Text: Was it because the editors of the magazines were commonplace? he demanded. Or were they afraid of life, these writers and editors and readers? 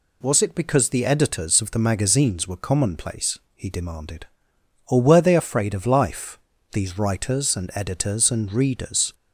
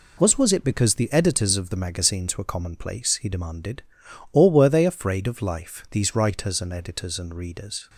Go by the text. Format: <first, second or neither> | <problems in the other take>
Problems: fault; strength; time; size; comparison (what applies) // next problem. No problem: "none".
first | says "Was" twice; at 0.3 s